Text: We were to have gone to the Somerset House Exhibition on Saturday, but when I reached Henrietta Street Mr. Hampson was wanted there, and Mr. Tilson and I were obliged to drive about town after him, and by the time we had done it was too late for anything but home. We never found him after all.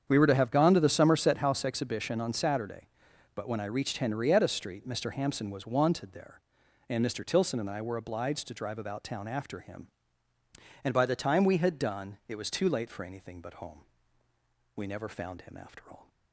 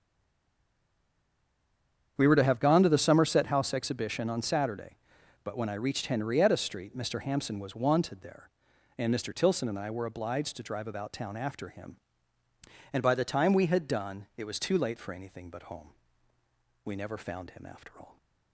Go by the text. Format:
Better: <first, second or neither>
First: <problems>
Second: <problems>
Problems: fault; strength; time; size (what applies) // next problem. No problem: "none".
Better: first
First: starts louder than the rest; strong; until 1.0 s; 8 dB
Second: stays silent before the first word; until 2.1 s; 2.1 s long // starts louder than the rest; strong; until 3.1 s; 8 dB